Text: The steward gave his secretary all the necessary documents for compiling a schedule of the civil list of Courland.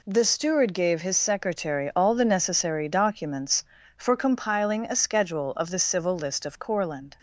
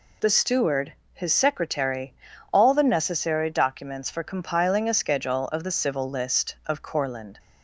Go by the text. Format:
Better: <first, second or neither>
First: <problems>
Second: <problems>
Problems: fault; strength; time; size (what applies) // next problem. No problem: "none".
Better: first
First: none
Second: skips "gave"; at 1.0 s // pauses between "secretary" and "all"; at 2.1 s; 0.40 s long